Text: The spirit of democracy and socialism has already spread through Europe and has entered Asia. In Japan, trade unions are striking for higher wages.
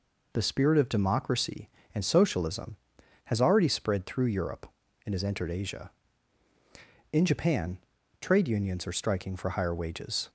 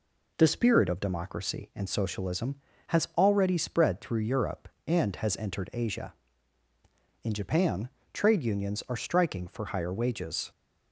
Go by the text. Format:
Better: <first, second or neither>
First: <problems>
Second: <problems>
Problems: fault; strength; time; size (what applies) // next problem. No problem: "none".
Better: neither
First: none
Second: none